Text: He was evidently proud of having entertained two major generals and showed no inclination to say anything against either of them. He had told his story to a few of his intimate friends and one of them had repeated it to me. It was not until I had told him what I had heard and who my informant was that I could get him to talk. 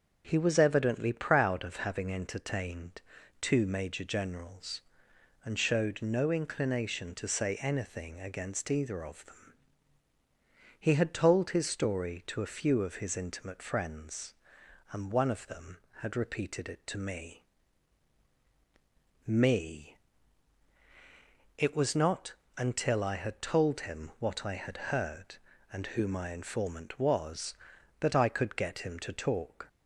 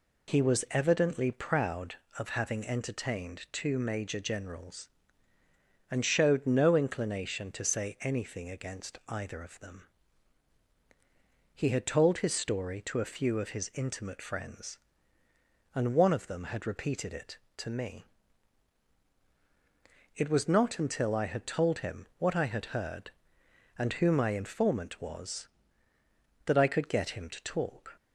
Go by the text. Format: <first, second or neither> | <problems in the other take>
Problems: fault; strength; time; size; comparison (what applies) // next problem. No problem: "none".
second | starts louder than the rest; until 1.2 s; 6.5 dB // pauses between "entertained" and "two"; at 2.9 s; 0.40 s long // says "me" twice; at 19.2 s // pauses between "not" and "until"; slight; at 22.3 s; 0.24 s long